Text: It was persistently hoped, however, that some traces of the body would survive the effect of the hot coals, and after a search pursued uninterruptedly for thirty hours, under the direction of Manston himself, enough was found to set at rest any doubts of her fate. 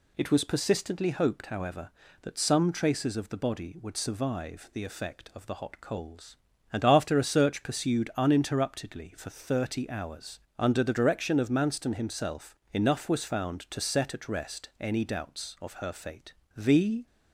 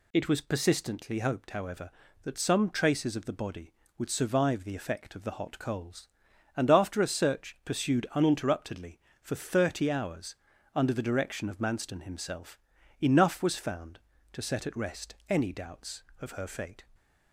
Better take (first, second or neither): second